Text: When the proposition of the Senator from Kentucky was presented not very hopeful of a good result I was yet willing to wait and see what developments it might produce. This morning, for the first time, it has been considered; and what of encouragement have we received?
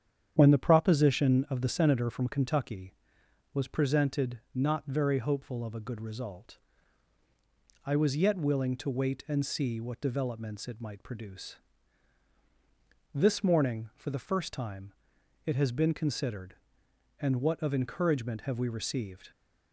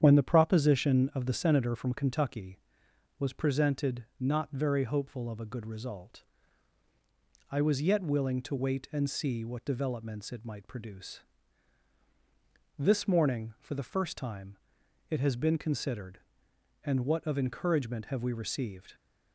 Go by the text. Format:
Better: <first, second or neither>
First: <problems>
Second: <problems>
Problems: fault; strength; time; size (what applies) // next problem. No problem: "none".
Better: neither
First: starts louder than the rest; strong; until 1.3 s; 9 dB // pauses between "result" and "I"; strong; at 6.5 s; 1.2 s long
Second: starts louder than the rest; strong; until 1.0 s; 9 dB // pauses between "result" and "I"; strong; at 6.2 s; 1.2 s long